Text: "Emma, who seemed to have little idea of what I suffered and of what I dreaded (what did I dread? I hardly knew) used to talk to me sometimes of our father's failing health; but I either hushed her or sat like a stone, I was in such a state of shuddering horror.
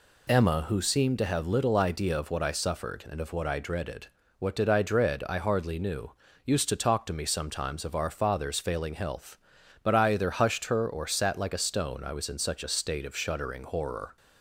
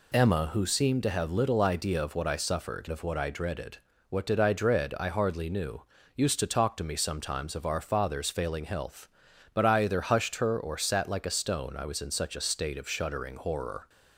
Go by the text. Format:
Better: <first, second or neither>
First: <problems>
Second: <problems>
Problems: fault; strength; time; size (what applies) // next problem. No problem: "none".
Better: first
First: none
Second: skips "and"; at 2.8 s